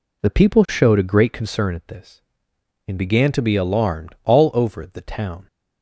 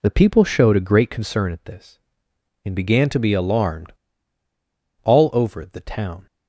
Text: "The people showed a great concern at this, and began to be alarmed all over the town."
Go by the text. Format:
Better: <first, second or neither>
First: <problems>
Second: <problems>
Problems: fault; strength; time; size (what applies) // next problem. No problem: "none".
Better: first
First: none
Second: pauses between "alarmed" and "all"; at 3.9 s; 1.1 s long